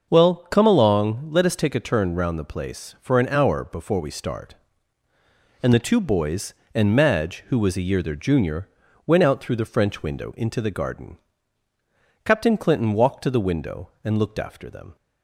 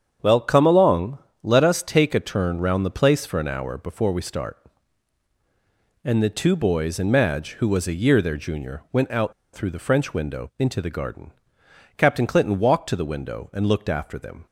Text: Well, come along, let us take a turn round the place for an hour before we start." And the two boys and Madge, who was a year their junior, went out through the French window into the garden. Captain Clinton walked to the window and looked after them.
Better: first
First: starts louder than the rest; noticeable; until 1.1 s; 6 dB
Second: starts louder than the rest; strong; until 1.4 s; 8 dB // pauses between "out" and "through"; slight; at 9.3 s; 0.20 s long

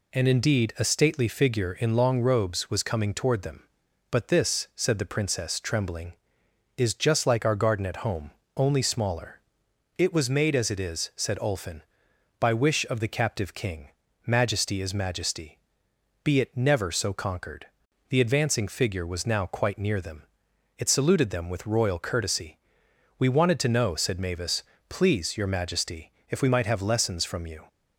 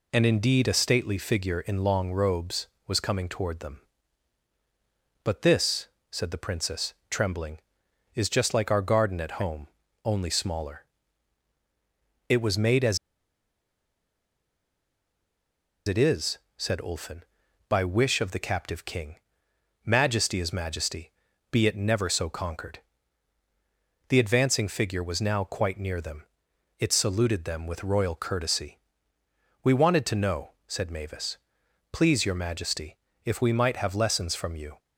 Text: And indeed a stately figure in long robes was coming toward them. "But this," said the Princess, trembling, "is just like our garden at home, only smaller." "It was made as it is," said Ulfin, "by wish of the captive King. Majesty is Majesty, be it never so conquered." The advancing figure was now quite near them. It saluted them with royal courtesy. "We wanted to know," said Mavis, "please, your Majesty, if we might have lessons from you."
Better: first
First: none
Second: pauses between "as" and "it"; strong; at 12.9 s; 2.8 s long

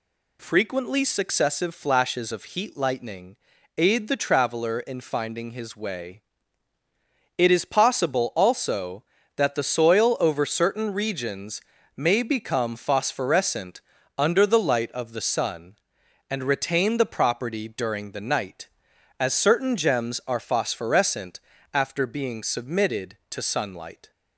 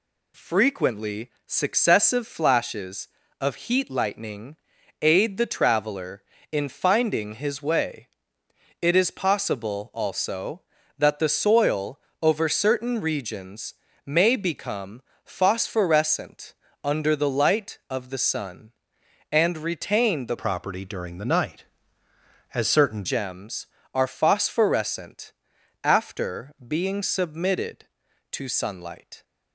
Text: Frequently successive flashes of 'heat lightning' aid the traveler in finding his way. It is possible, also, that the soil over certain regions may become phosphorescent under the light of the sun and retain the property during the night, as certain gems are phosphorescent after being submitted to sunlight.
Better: first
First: pauses between "lightning" and "aid"; at 3.3 s; 0.40 s long // pauses between "regions" and "may"; slight; at 11.6 s; 0.36 s long // pauses between "phosphorescent" and "under"; slight; at 13.8 s; 0.36 s long // pauses between "phosphorescent" and "after"; slight; at 21.4 s; 0.34 s long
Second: pauses between "Frequently" and "successive"; slight; at 1.3 s; 0.16 s long // pauses between "lightning" and "aid"; at 4.5 s; 0.44 s long // pauses between "soil" and "over"; slight; at 12.0 s; 0.20 s long // pauses between "regions" and "may"; slight; at 13.7 s; 0.30 s long // pauses between "become" and "phosphorescent"; slight; at 15.0 s; 0.22 s long // pauses between "phosphorescent" and "under"; slight; at 16.5 s; 0.30 s long // changes voice from "property" to "certain"; from 20.3 to 23.0 s; 2.7 s long // pauses between "phosphorescent" and "after"; noticeable; at 25.3 s; 0.50 s long

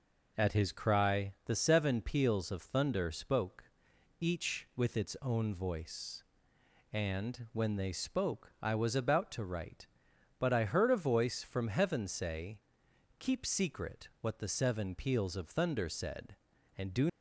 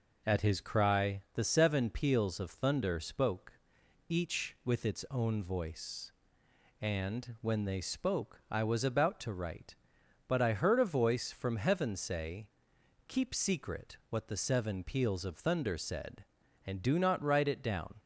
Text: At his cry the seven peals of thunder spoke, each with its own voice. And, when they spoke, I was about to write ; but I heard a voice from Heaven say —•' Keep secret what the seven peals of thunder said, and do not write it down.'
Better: second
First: stops before "not write it down"; at 17.0 s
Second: none

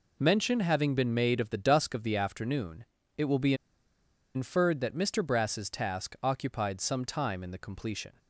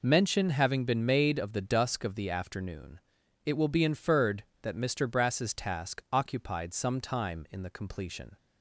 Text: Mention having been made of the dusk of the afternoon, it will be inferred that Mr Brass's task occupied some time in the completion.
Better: second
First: pauses between "be" and "inferred"; noticeable; at 3.5 s; 0.81 s long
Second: none

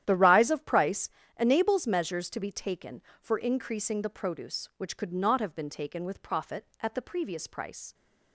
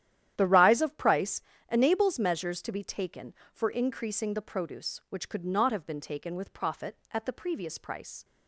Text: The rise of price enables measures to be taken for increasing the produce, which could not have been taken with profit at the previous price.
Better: neither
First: starts louder than the rest; strong; until 1.0 s; 11 dB // pauses between "price" and "enables"; slight; at 1.0 s; 0.32 s long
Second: starts louder than the rest; strong; until 1.3 s; 11 dB // pauses between "price" and "enables"; slight; at 1.3 s; 0.32 s long

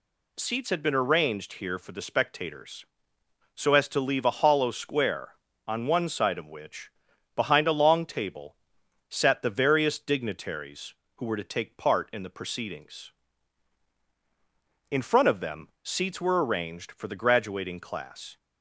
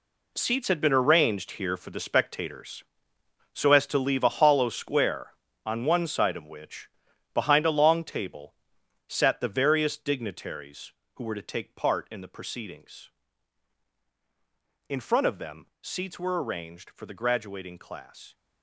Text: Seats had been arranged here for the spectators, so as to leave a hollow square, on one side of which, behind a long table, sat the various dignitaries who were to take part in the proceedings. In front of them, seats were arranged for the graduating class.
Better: first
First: none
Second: gets quieter; strong; throughout; 11.5 dB

